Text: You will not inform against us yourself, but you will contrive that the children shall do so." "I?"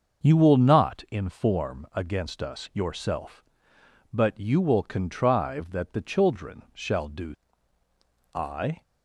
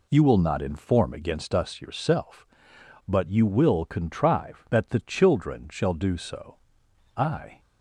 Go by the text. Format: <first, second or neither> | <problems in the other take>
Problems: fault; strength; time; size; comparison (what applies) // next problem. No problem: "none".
second | starts louder than the rest; until 1.2 s; 6 dB // skips "so"; at 7.8 s